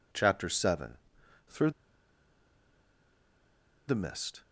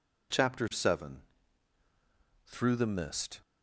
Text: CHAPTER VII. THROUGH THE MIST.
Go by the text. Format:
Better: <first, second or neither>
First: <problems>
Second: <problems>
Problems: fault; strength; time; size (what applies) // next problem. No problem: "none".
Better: second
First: pauses between "THROUGH" and "THE"; strong; at 1.7 s; 2.1 s long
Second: none